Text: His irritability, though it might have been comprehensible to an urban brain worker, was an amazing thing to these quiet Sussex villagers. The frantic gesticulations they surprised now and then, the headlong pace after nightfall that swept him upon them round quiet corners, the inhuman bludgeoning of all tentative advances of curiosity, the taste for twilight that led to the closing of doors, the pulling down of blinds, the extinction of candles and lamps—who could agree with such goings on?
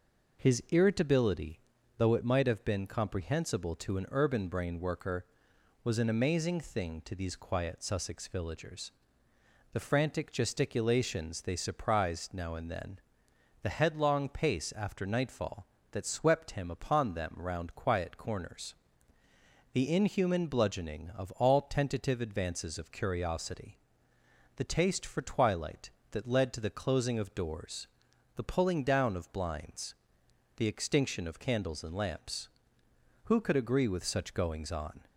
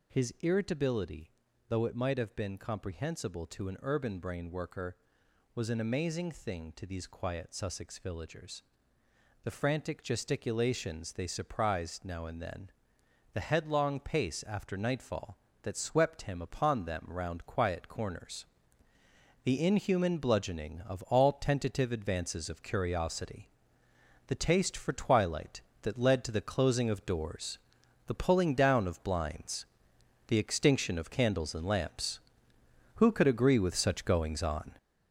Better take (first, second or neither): first